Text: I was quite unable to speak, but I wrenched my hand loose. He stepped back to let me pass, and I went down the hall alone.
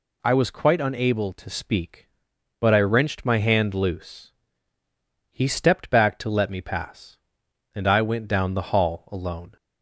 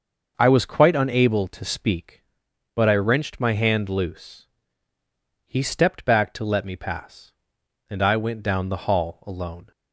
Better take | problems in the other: first | starts louder than the rest; noticeable; until 2.1 s; 6 dB

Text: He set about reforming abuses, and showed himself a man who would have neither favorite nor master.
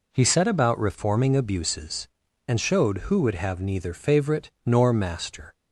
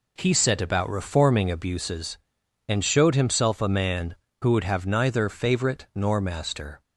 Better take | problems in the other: second | skips "himself a man"; at 2.9 s

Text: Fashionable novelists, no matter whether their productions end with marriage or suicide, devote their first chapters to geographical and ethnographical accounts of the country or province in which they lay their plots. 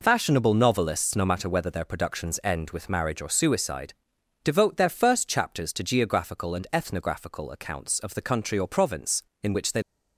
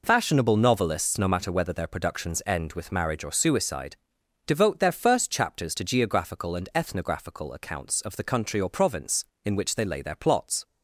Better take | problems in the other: second | stops before "lay their plots"; at 9.8 s

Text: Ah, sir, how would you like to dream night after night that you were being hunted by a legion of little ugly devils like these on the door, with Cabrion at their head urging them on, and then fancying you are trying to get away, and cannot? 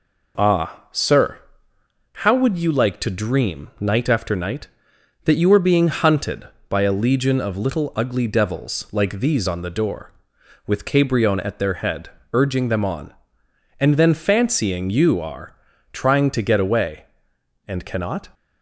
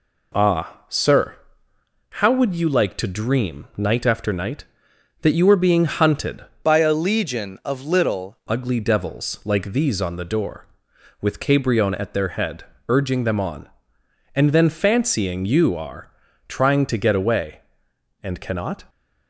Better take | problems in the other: first | changes voice from "by" to "little"; from 6.6 to 8.3 s; 1.7 s long // pauses between "head" and "urging"; slight; at 12.6 s; 0.26 s long; slight in the first // pauses between "are" and "trying"; slight; at 16.1 s; 0.36 s long; slight in the first

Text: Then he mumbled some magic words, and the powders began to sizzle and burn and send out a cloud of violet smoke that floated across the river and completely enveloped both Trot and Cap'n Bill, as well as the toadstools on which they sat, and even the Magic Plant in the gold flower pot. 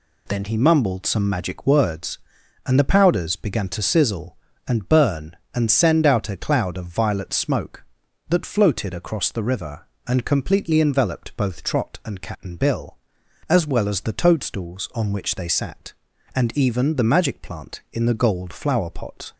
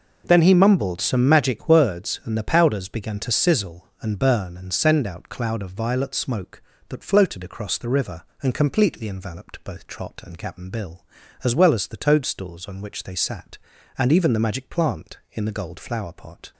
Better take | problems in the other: first | skips "a"; at 5.2 s

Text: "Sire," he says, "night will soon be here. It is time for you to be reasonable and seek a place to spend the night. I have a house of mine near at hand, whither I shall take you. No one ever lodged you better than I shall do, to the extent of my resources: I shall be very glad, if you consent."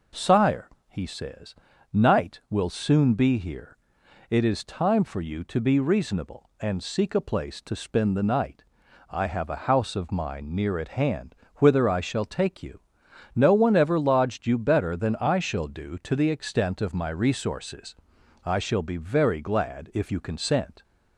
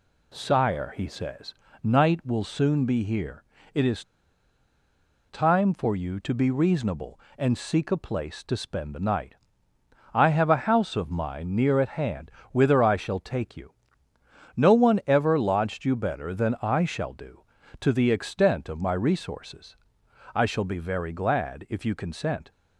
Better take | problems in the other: first | pauses between "is" and "time"; strong; at 4.0 s; 1.2 s long

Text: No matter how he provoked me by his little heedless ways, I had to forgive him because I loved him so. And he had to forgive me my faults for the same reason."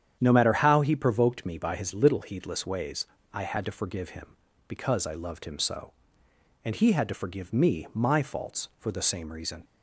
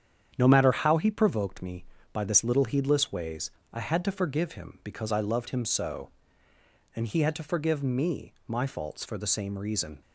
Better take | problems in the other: first | starts louder than the rest; strong; until 1.3 s; 8.5 dB; strong in the first // says "this" for "his"; at 2.2 s // pauses between "me" and "my"; slight; at 8.3 s; 0.16 s long

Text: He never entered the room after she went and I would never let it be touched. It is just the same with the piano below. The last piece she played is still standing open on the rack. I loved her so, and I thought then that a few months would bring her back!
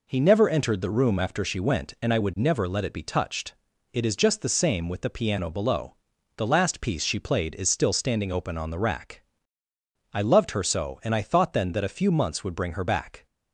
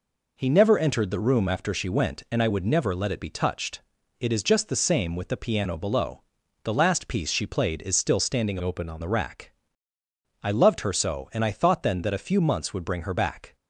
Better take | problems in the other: first | changes voice from "open" to "on"; from 8.6 to 9.0 s; 0.4 s long

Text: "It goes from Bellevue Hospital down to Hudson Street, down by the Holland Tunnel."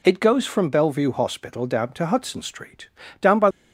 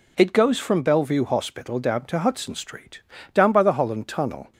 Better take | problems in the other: second | stops before "the Holland Tunnel"; at 3.5 s

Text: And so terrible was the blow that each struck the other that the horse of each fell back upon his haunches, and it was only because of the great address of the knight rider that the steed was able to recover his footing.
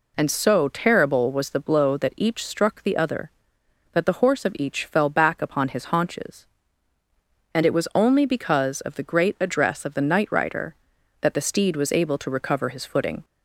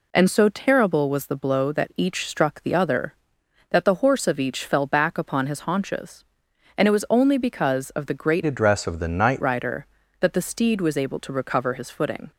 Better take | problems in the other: first | changes voice from "address" to "knight"; from 8.4 to 9.4 s; 1.0 s long

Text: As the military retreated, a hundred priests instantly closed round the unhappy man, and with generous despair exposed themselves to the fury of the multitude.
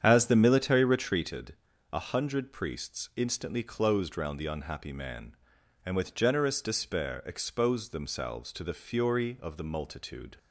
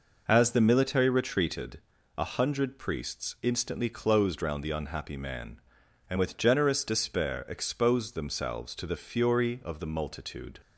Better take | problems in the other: second | starts louder than the rest; strong; until 1.1 s; 8.5 dB

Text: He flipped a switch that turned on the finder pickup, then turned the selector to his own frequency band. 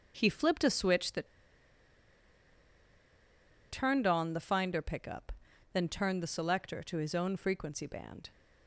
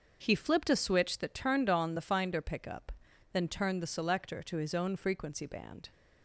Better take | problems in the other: second | starts louder than the rest; noticeable; until 1.1 s; 6 dB; also in the second // pauses between "that" and "turned"; strong; at 1.2 s; 2.4 s long

